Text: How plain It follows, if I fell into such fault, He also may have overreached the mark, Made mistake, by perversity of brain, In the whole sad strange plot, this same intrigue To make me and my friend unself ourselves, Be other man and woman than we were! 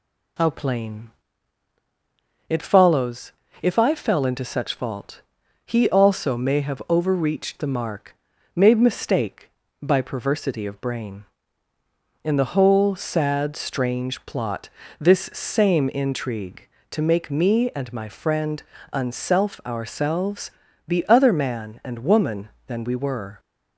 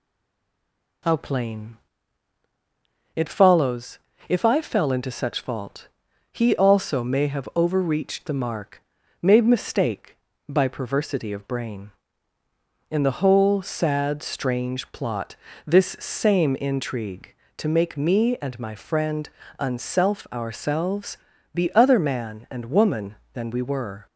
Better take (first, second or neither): first